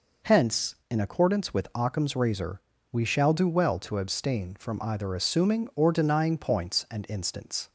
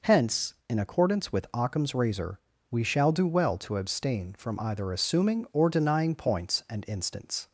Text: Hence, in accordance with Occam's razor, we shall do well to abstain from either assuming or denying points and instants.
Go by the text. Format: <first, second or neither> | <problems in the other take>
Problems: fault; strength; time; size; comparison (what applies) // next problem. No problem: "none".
neither | none